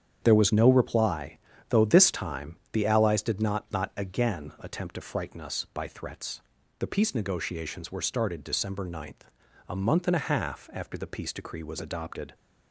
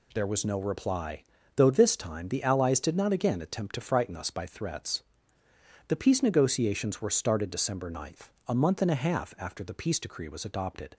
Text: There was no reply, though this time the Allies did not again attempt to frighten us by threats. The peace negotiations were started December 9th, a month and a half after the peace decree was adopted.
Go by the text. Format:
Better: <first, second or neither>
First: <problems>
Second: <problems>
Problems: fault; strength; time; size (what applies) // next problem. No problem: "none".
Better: second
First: starts louder than the rest; strong; until 1.2 s; 8.5 dB // says "not" twice; at 3.7 s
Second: none